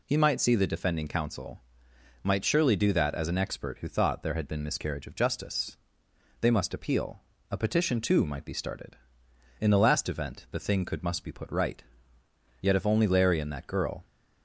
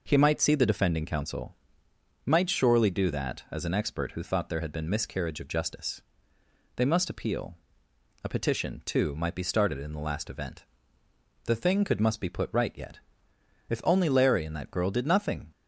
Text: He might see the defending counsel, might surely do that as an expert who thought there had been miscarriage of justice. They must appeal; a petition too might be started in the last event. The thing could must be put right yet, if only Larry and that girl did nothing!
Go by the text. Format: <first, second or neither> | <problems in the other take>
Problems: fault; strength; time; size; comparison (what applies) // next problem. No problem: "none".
second | pauses between "right" and "yet"; noticeable; at 11.8 s; 0.76 s long // stops before "did nothing"; at 14.0 s